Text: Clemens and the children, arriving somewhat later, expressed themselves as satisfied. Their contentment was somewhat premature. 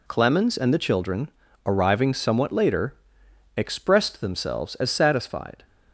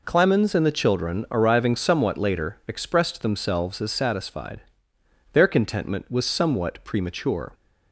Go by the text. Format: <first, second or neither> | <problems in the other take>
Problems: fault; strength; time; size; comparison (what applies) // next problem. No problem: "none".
second | stops before "Their contentment was somewhat premature"; at 5.6 s